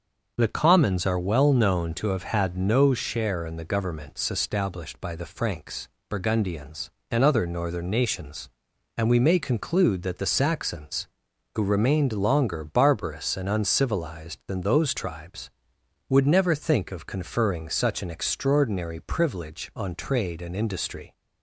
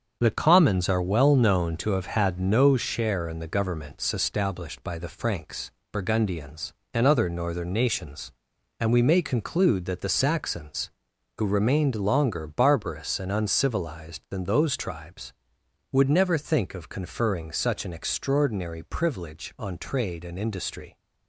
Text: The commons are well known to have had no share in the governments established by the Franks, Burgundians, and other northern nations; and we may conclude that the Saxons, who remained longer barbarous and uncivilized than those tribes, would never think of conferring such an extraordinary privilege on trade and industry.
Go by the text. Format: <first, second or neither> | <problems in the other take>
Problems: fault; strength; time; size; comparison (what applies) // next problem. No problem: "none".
first | gets quieter; throughout; 6 dB // starts louder than the rest; until 1.2 s; 7 dB; also in the first